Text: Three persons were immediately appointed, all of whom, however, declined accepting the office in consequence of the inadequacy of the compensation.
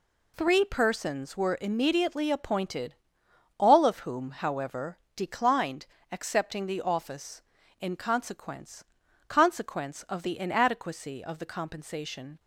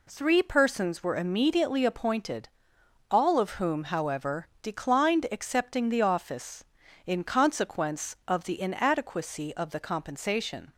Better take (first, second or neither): second